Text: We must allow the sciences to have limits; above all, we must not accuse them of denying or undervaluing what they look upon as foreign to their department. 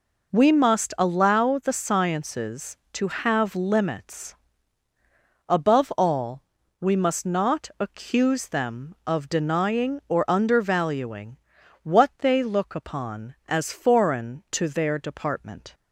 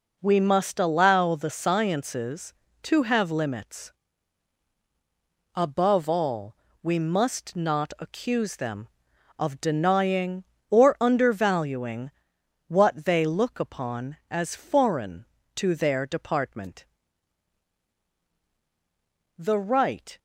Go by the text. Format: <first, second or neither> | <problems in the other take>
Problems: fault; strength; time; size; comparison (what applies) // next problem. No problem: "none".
first | pauses between "undervaluing" and "what"; noticeable; at 12.0 s; 0.56 s long; noticeable in the first // goes on to say "The right"; noticeable; from 19.3 s on; 0.80 s long